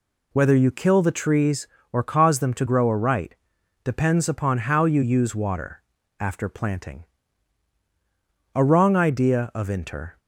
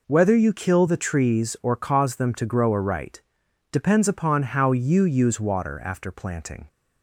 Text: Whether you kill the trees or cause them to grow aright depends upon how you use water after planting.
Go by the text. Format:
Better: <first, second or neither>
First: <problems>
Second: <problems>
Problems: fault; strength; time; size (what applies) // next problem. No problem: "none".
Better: second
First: pauses between "aright" and "depends"; noticeable; at 3.3 s; 0.48 s long // pauses between "water" and "after"; at 5.8 s; 0.38 s long // goes on to say "A Wrong Idea of Inter"; from 8.5 s on; 1.6 s long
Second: pauses between "aright" and "depends"; noticeable; at 3.2 s; 0.50 s long